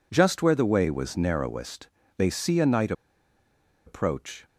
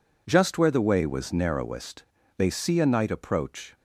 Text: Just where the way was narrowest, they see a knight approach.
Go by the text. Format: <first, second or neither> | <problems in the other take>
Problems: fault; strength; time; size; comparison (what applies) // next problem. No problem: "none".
second | pauses between "knight" and "approach"; noticeable; at 2.9 s; 0.93 s long